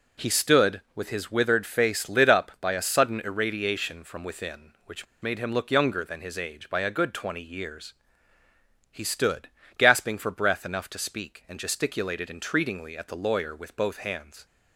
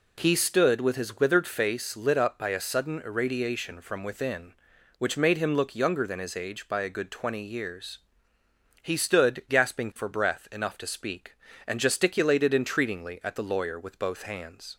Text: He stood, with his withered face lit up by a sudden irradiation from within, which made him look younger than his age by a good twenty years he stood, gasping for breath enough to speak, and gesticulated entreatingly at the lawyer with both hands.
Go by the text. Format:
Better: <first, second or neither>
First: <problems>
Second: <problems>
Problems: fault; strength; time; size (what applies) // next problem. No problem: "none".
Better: second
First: pauses between "which" and "made"; slight; at 5.0 s; 0.17 s long // pauses between "years" and "he"; noticeable; at 7.9 s; 0.98 s long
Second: pauses between "years" and "he"; noticeable; at 7.9 s; 0.82 s long